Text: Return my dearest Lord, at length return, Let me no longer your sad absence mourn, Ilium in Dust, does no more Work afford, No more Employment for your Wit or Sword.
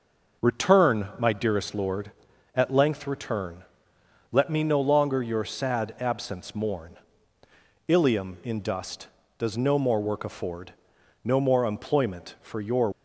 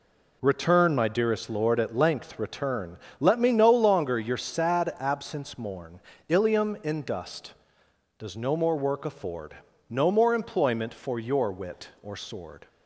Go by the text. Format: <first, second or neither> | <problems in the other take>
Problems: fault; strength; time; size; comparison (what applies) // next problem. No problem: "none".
second | stops before "Wit or Sword"; at 12.9 s